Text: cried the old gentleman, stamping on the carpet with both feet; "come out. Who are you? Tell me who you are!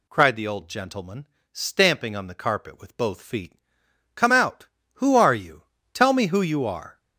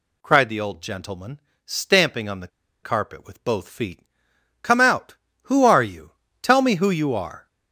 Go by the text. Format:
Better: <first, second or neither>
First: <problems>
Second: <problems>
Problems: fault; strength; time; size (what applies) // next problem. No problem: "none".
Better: first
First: none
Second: pauses between "the" and "carpet"; slight; at 2.4 s; 0.35 s long